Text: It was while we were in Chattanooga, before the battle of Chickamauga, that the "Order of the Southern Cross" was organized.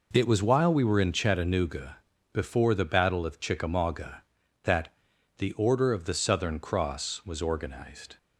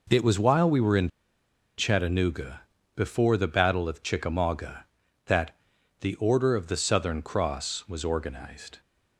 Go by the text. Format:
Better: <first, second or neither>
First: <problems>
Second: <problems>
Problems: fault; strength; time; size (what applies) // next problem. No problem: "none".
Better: first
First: pauses between "that" and "the"; noticeable; at 4.9 s; 0.46 s long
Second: pauses between "in" and "Chattanooga"; noticeable; at 1.1 s; 0.67 s long // pauses between "that" and "the"; noticeable; at 5.5 s; 0.46 s long